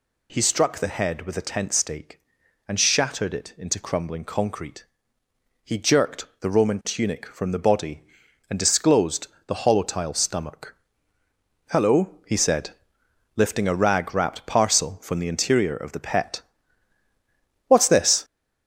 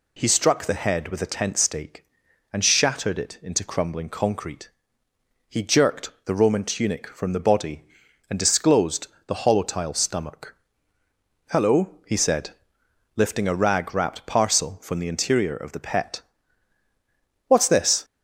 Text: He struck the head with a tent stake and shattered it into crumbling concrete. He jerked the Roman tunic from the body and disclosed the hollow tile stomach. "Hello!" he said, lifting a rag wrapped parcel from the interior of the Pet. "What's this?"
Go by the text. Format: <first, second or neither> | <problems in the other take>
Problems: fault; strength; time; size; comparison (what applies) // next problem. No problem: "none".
second | gets louder; noticeable; throughout; 5.5 dB // pauses between "disclosed" and "the"; slight; at 9.2 s; 0.18 s long; slight in the second